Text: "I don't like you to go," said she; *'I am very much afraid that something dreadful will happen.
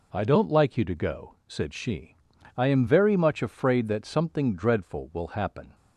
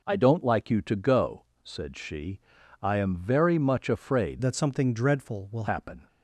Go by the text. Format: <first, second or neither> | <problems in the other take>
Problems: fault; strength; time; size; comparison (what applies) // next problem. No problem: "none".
first | changes voice from "that" to "will"; from 4.4 to 5.6 s; 1.2 s long